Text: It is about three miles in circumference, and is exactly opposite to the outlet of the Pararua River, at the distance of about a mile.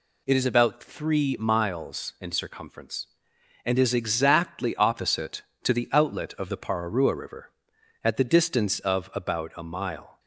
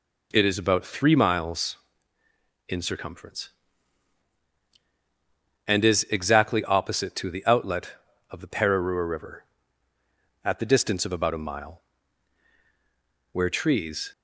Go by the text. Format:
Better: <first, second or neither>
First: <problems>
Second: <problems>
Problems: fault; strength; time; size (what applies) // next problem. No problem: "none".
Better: first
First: none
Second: goes on to say "Where trees"; noticeable; from 13.3 s on; 0.80 s long